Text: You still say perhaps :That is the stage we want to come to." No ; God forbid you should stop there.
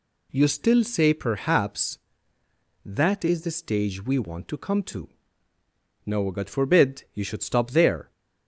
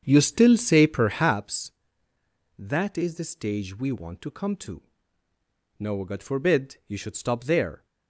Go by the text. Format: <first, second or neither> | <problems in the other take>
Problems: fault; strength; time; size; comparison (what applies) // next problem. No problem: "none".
first | starts louder than the rest; strong; until 1.4 s; 7.5 dB